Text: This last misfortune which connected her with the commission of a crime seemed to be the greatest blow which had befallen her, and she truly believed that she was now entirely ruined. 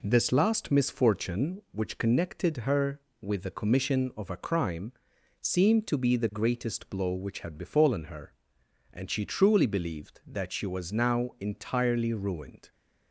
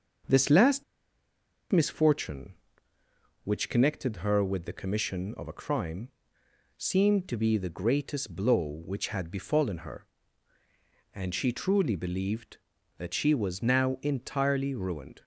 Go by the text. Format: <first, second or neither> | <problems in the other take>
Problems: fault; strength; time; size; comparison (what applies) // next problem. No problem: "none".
first | starts louder than the rest; until 2.1 s; 6.5 dB // pauses between "last" and "misfortune"; noticeable; at 0.8 s; 0.89 s long // pauses between "crime" and "seemed"; noticeable; at 6.0 s; 0.70 s long; noticeable in the first